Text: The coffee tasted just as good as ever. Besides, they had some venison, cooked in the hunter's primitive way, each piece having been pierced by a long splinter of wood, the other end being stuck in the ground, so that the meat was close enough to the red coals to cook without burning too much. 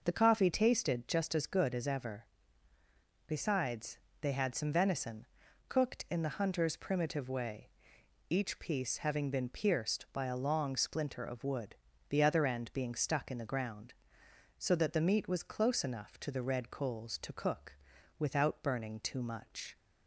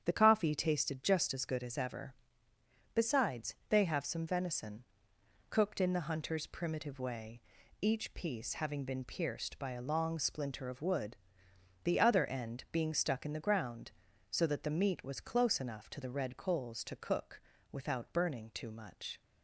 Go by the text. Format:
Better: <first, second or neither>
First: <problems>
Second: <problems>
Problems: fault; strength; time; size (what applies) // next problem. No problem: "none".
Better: first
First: pauses between "cook" and "without"; at 17.7 s; 0.42 s long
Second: starts louder than the rest; strong; until 1.0 s; 8.5 dB // says "have" for "had"; at 3.8 s // pauses between "cook" and "without"; slight; at 17.3 s; 0.32 s long